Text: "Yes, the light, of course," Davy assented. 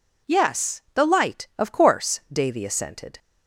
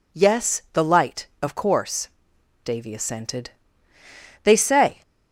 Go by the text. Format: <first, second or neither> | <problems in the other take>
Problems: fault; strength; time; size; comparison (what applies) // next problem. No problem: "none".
first | goes on to say "They say"; from 4.4 s on; 0.58 s long